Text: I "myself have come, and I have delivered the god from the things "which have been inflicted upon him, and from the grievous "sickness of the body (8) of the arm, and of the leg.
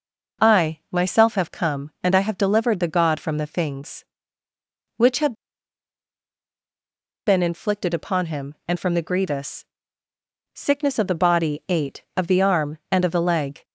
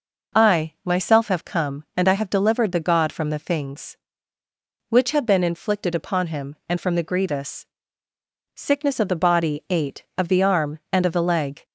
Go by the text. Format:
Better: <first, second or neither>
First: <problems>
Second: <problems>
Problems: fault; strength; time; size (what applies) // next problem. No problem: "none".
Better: second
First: pauses between "have" and "been"; strong; at 5.3 s; 1.9 s long // pauses between "grievous" and "sickness"; noticeable; at 9.6 s; 0.90 s long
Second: pauses between "grievous" and "sickness"; noticeable; at 7.6 s; 0.90 s long